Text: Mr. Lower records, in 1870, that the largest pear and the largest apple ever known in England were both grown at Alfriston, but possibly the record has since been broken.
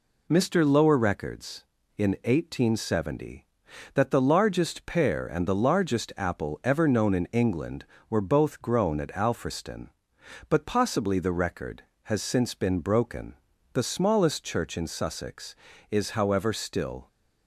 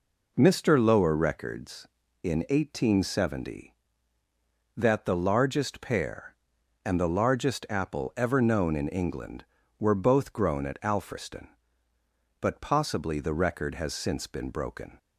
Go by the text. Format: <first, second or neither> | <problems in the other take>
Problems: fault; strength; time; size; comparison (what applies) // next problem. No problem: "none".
second | goes on to say "The smallest church in Sussex is however still"; strong; from 13.7 s on; 3.3 s long